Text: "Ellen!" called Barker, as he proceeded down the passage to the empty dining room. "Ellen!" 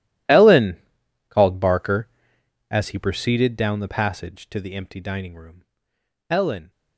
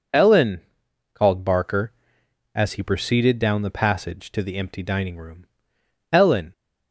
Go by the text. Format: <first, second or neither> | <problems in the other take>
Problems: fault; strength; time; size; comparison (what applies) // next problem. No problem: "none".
second | gets quieter; strong; throughout; 19 dB